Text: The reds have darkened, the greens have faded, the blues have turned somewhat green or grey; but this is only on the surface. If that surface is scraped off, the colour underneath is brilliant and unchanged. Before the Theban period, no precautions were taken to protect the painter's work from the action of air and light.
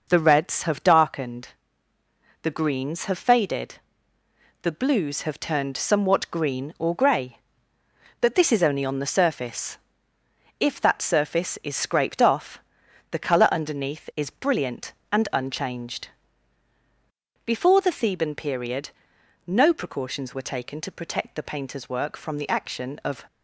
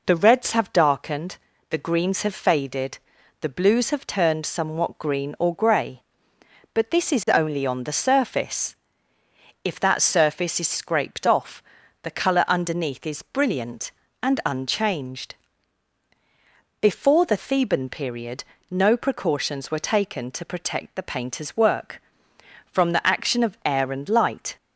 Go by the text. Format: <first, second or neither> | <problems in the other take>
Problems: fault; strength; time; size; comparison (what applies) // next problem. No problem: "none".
second | stops before "air and light"; at 23.2 s